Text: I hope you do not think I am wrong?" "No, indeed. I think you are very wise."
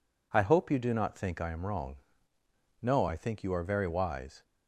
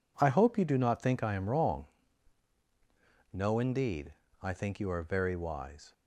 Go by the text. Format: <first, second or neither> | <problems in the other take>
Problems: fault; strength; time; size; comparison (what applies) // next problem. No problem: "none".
second | skips "indeed"; at 3.0 s